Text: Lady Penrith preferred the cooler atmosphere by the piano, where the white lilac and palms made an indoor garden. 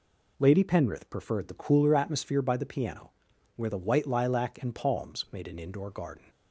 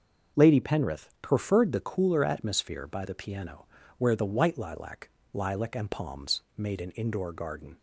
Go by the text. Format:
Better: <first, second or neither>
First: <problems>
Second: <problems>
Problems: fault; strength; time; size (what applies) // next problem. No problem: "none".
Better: first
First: none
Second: starts louder than the rest; until 1.4 s; 6.5 dB // says "lilac" twice; at 5.3 s // pauses between "palms" and "made"; slight; at 6.4 s; 0.16 s long